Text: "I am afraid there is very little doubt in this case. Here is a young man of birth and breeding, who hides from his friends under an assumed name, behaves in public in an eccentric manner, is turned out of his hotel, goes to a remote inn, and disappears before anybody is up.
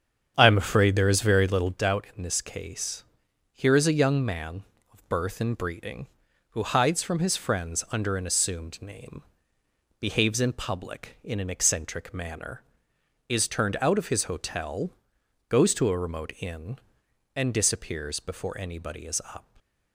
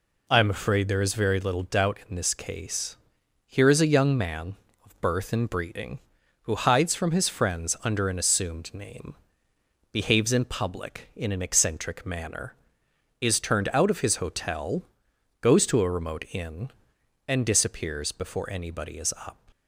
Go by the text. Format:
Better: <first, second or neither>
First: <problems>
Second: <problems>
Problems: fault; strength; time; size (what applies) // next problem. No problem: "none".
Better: second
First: starts louder than the rest; strong; until 1.8 s; 8 dB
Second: none